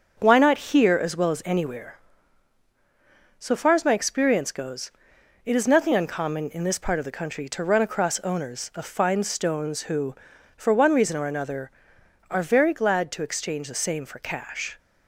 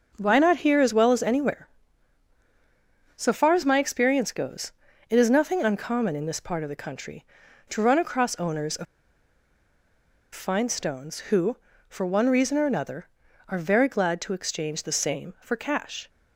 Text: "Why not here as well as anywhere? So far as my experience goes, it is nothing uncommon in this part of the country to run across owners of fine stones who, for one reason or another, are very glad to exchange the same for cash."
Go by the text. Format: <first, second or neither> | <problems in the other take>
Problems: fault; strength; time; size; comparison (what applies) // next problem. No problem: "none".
first | starts louder than the rest; noticeable; until 1.1 s; 6 dB; also in the first // pauses between "of" and "fine"; strong; at 8.8 s; 1.4 s long